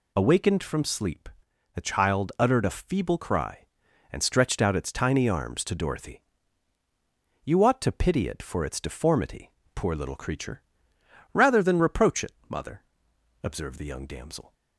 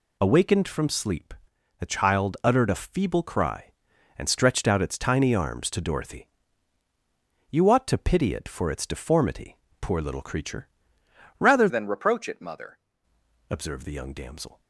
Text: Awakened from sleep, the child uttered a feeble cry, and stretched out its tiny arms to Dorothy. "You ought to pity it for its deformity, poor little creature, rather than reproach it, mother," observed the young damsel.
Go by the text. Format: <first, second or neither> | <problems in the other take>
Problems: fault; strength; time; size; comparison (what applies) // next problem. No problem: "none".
first | changes voice from "than" to "mother"; from 11.7 to 12.7 s; 1.0 s long